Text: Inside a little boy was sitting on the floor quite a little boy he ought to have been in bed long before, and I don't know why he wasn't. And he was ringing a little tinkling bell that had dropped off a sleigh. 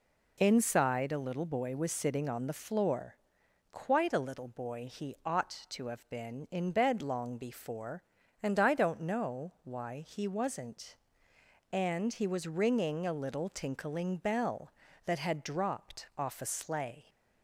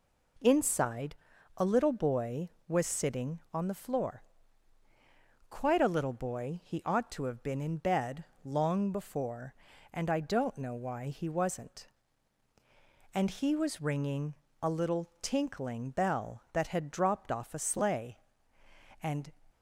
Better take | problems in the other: first | pauses between "Inside" and "a"; at 1.1 s; 0.42 s long // pauses between "floor" and "quite"; strong; at 4.2 s; 1.2 s long; noticeable in the first // pauses between "bed" and "long"; slight; at 8.2 s; 0.18 s long // pauses between "ringing" and "a"; slight; at 14.3 s; 0.28 s long // goes on to say "And"; slight; from 19.0 s on; 0.30 s long

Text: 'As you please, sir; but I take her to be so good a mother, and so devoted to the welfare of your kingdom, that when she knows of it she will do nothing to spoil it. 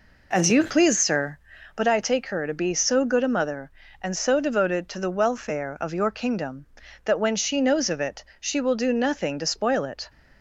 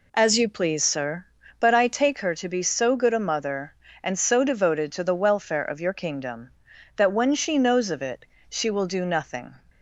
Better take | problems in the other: first | pauses between "it" and "she"; slight; at 8.2 s; 0.24 s long; slight in the first // stops before "to spoil it"; at 9.6 s

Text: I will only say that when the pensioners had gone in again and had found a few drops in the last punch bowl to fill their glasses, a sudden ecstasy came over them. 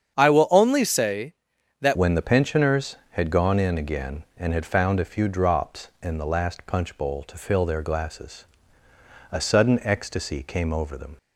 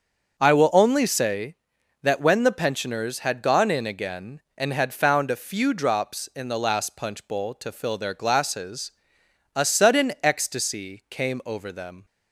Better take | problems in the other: second | starts louder than the rest; strong; until 1.2 s; 8 dB; also in the second // changes voice at "when"; from 1.9 s on; 9.2 s long

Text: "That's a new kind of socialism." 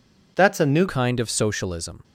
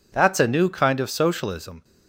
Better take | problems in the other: second | changes voice at "kind"; from 0.8 s on; 1.2 s long

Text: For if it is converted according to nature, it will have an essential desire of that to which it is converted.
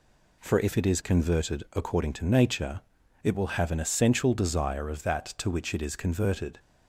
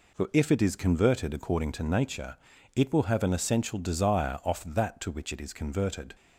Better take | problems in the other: first | says "off" for "of"; at 4.4 s

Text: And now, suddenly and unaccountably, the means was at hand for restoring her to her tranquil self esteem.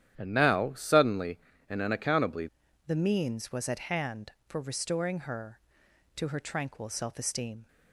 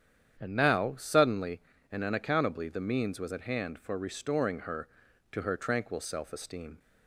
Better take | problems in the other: second | starts louder than the rest; strong; until 1.1 s; 10.5 dB; strong in the second // changes voice at "the"; from 2.8 s on; 4.8 s long

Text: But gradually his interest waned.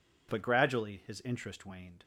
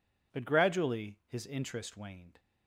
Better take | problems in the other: neither | none

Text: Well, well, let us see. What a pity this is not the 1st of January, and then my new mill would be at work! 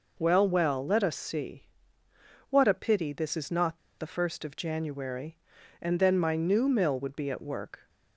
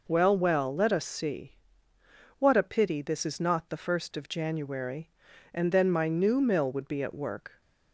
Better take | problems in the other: second | pauses between "not" and "the"; slight; at 3.7 s; 0.21 s long

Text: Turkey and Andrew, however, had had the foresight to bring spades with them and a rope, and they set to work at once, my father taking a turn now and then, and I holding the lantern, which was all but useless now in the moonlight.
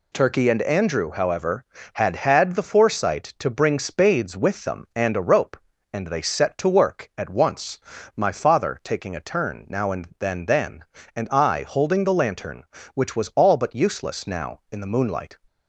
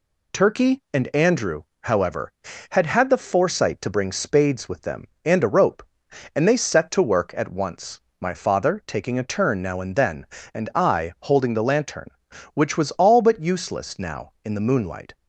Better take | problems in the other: second | says "then" twice; at 10.4 s

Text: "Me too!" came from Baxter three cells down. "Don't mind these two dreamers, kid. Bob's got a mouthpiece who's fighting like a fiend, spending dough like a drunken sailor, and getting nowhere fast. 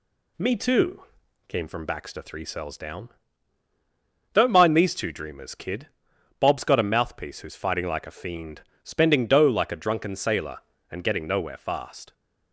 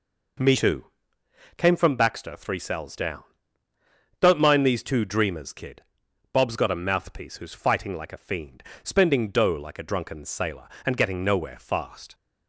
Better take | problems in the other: neither | none

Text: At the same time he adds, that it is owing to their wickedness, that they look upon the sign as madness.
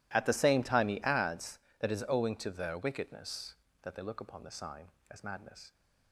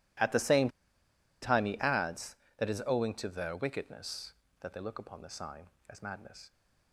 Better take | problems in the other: first | pauses between "same" and "time"; noticeable; at 0.6 s; 0.73 s long

